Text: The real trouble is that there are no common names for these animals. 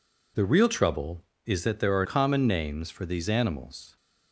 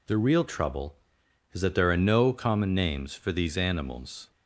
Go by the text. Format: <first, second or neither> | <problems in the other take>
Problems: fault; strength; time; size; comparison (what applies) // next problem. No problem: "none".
second | skips "no"; at 2.0 s